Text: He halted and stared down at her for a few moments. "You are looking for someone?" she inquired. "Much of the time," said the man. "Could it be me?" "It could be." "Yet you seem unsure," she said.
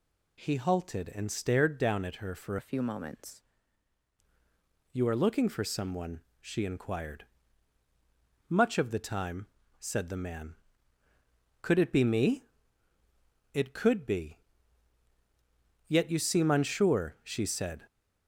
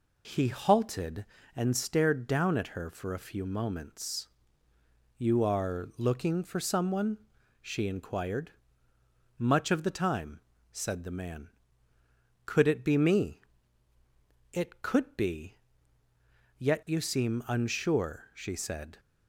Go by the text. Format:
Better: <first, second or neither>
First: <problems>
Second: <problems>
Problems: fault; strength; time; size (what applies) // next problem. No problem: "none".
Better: second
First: changes voice from "a" to "moments"; from 2.5 to 3.4 s; 0.9 s long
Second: none